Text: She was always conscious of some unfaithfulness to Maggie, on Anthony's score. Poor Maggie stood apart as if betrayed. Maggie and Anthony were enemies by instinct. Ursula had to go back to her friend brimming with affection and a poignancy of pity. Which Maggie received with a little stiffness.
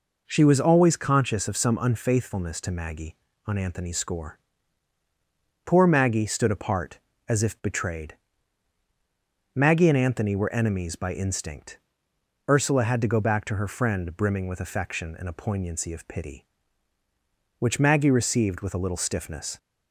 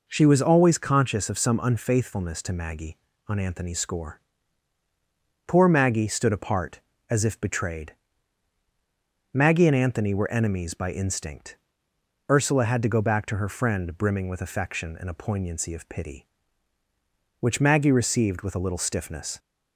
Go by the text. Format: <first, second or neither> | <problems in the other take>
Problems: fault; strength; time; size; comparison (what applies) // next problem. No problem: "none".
neither | none